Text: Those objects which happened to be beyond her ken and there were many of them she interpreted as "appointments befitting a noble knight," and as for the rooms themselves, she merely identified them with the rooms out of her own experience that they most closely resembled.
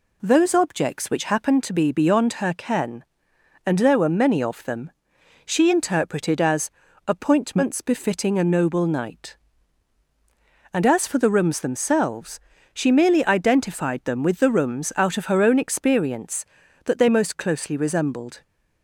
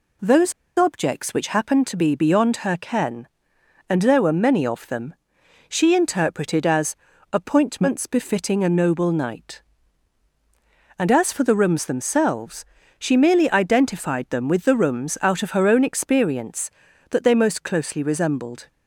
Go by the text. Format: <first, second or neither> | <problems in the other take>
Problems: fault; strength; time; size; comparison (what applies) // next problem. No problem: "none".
first | pauses between "Those" and "objects"; slight; at 0.5 s; 0.24 s long // pauses between "them" and "she"; noticeable; at 5.1 s; 0.56 s long; noticeable in the first // pauses between "as" and "appointments"; at 6.9 s; 0.38 s long; also in the first